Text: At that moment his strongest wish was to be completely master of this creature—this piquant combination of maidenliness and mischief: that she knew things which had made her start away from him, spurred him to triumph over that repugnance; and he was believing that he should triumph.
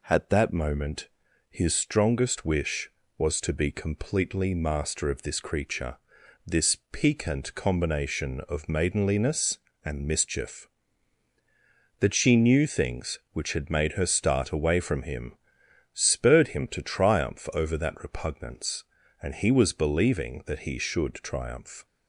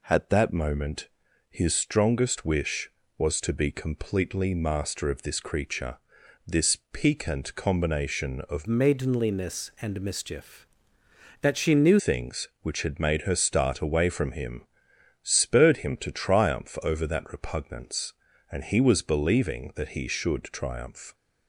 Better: first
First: pauses between "moment" and "his"; at 1.0 s; 0.42 s long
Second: pauses between "moment" and "his"; at 1.0 s; 0.42 s long // changes voice from "maidenliness" to "knew"; from 8.6 to 12.0 s; 3.4 s long

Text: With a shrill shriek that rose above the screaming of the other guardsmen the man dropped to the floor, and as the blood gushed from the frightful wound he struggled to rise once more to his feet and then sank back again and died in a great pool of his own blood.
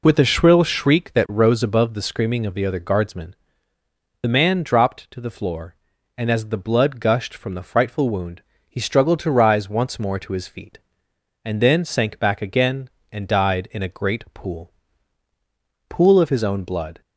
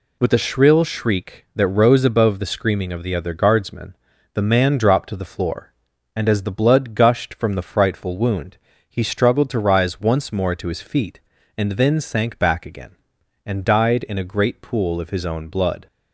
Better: second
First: pauses between "guardsmen" and "the"; noticeable; at 3.3 s; 0.88 s long // pauses between "wound" and "he"; slight; at 8.4 s; 0.28 s long // says "pool" twice; at 15.8 s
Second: pauses between "guardsmen" and "the"; at 3.9 s; 0.40 s long // pauses between "wound" and "he"; slight; at 8.5 s; 0.32 s long

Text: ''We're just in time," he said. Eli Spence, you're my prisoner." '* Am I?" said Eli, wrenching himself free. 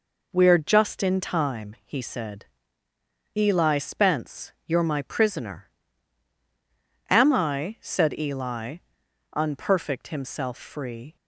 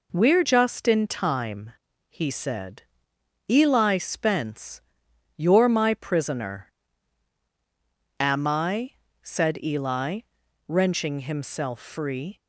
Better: second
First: says "unperfect" for "wrenching"; at 9.3 s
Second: none

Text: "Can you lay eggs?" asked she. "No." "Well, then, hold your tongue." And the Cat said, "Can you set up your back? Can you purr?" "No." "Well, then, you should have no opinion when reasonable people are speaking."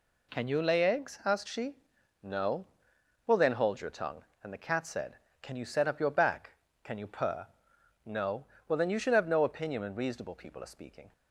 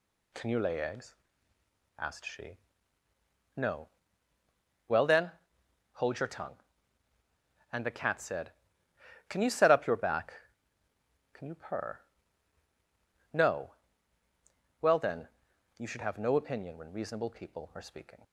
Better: neither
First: none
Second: none

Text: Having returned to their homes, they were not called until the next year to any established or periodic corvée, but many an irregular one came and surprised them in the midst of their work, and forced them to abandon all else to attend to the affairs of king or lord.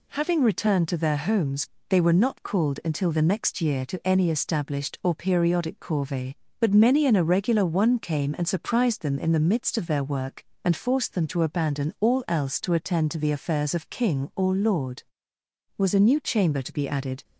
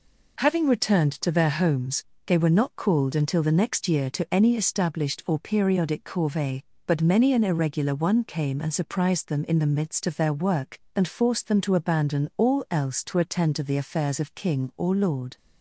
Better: second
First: goes on to say "Was a new chamber to be added"; from 15.7 s on; 1.4 s long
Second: none

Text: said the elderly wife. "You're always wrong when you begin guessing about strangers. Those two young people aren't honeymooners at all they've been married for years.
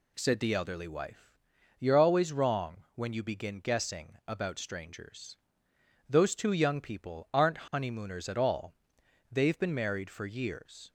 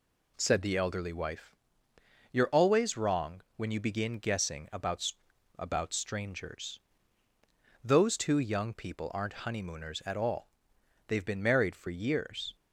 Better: first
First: pauses between "all" and "they've"; noticeable; at 8.7 s; 0.58 s long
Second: says "about" twice; at 5.5 s // pauses between "all" and "they've"; noticeable; at 10.4 s; 0.60 s long

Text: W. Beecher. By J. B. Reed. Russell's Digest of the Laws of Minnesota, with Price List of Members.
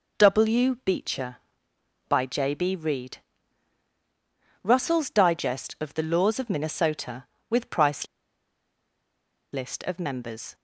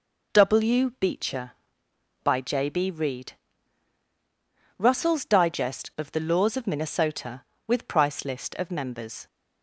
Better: second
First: pauses between "Price" and "List"; strong; at 8.0 s; 1.4 s long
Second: none

